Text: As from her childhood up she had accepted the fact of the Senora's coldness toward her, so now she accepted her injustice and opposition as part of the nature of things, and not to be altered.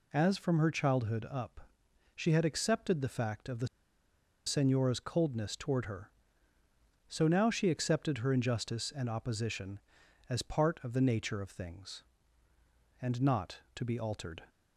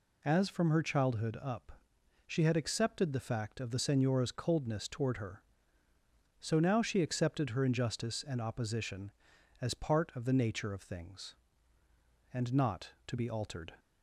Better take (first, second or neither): second